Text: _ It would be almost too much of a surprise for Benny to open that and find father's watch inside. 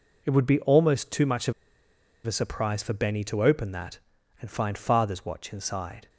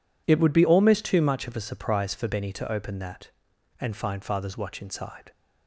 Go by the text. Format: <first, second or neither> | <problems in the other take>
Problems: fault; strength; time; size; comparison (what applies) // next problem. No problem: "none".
second | pauses between "of" and "a"; noticeable; at 1.5 s; 0.73 s long